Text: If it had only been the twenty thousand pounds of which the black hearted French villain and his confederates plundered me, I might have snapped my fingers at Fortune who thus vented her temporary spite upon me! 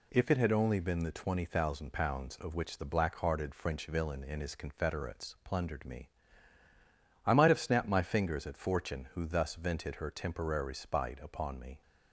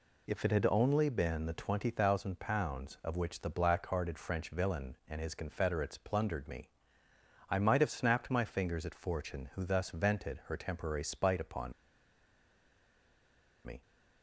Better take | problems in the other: first | pauses between "upon" and "me"; strong; at 11.7 s; 1.9 s long

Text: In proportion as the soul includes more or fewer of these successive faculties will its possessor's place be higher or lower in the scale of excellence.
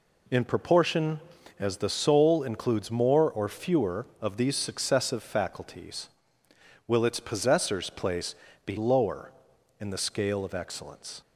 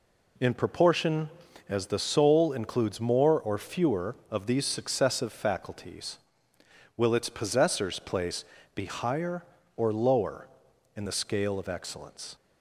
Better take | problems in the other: second | pauses between "place" and "be"; slight; at 8.3 s; 0.30 s long; slight in the second // skips "higher or"; at 8.7 s

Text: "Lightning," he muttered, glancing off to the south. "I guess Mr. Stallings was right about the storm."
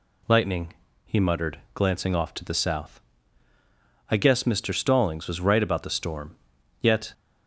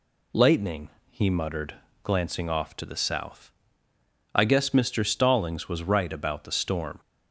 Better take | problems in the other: second | goes on to say "Yet"; slight; from 6.7 s on; 0.34 s long

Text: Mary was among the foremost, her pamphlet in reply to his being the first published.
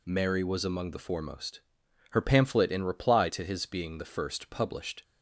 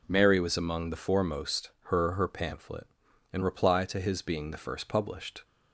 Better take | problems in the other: first | says "her" twice; at 2.1 s

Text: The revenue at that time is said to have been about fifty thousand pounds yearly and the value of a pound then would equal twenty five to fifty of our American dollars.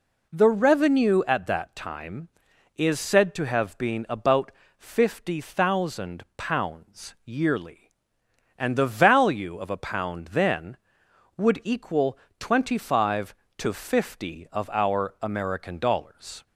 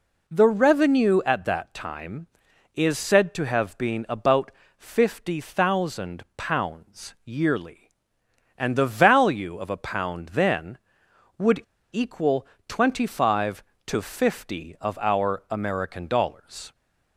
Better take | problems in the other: first | pauses between "about" and "fifty"; slight; at 4.5 s; 0.26 s long; slight in the first // pauses between "would" and "equal"; slight; at 11.6 s; 0.31 s long // pauses between "equal" and "twenty"; slight; at 12.4 s; 0.22 s long; slight in the first

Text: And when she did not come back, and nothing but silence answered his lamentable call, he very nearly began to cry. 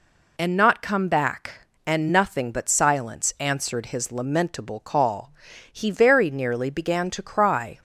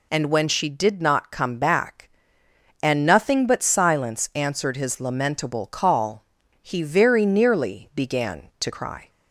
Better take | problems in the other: second | skips "when she did"; at 0.5 s

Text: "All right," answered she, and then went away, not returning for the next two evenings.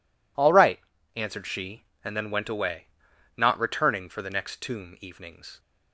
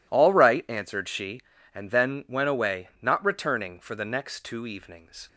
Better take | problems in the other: second | says "tomb" for "two"; at 4.6 s

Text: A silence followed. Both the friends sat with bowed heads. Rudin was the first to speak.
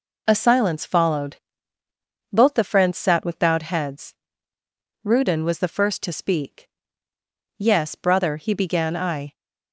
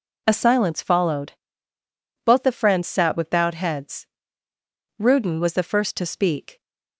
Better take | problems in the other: second | goes on to say "Yes brother he began I"; strong; from 7.5 s on; 1.7 s long

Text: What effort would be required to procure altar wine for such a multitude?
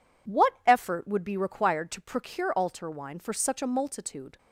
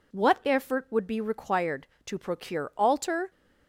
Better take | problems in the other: first | stops before "wine for such a multitude"; at 3.3 s

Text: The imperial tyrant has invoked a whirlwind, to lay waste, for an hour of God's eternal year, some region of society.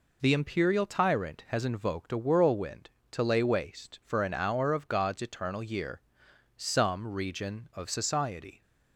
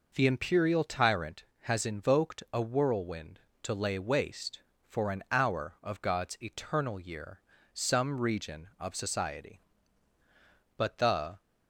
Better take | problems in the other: first | goes on to say "But the"; noticeable; from 10.7 s on; 0.66 s long

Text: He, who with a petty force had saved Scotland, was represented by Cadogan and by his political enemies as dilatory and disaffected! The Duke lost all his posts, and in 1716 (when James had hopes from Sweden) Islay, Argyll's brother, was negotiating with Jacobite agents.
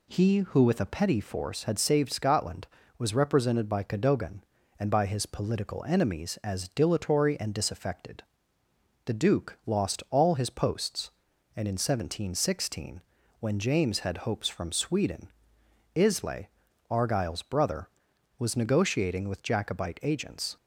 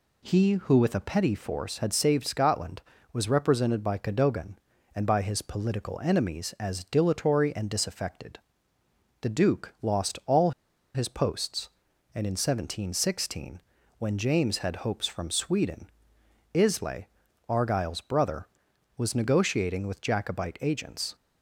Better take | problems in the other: first | pauses between "all" and "his"; at 10.5 s; 0.43 s long

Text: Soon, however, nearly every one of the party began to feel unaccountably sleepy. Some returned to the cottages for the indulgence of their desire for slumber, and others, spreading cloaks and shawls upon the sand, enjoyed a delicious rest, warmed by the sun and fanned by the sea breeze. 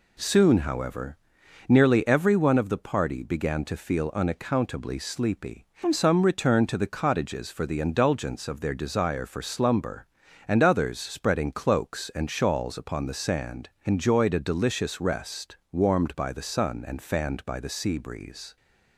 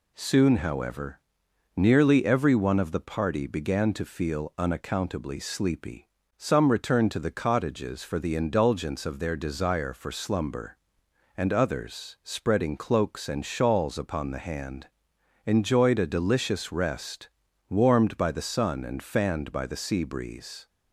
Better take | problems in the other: first | says "hand" for "sand"; at 14.3 s

